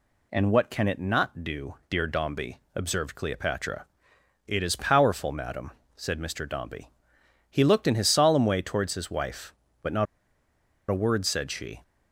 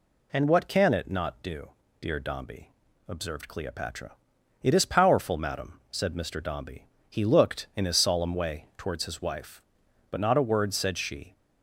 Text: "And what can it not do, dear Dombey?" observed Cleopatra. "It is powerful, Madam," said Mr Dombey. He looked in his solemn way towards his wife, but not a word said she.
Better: second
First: pauses between "not" and "a"; noticeable; at 10.0 s; 0.84 s long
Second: none

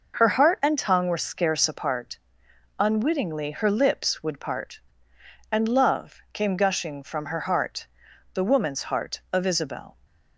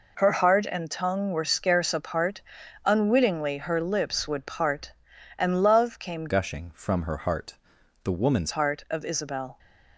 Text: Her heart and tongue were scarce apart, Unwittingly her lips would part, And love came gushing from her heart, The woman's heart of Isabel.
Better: first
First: none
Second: changes voice from "gushing" to "woman's"; from 6.2 to 8.5 s; 2.3 s long

